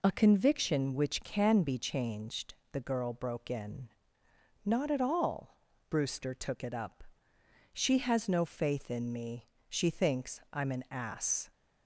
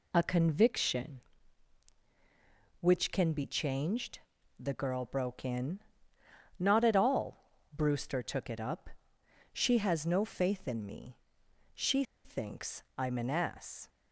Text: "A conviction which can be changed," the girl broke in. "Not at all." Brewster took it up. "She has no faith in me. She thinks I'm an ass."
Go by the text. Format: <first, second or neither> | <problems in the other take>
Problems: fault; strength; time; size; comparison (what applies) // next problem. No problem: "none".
first | pauses between "She" and "thinks"; slight; at 12.0 s; 0.21 s long